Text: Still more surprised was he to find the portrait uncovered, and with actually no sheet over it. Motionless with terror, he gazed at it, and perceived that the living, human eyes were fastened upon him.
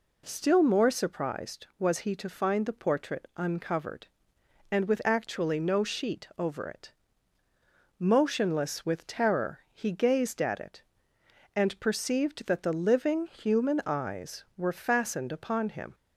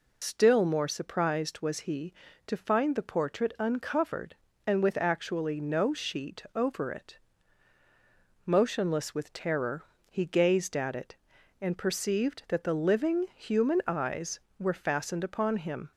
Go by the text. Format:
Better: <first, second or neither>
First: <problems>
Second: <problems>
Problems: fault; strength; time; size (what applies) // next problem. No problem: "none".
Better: first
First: none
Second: loses the start of "Still"; at 0.2 s; 105 ms